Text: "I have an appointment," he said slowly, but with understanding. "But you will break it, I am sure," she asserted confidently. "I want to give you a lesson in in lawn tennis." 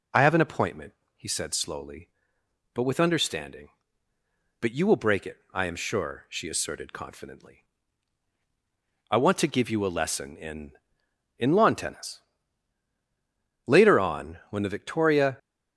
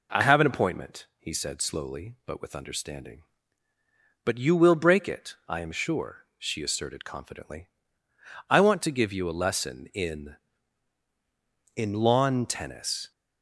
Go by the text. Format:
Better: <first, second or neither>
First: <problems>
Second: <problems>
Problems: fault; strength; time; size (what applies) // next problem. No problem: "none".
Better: second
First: goes on to say "Later on when the victoria"; strong; from 13.6 s on; 1.7 s long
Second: none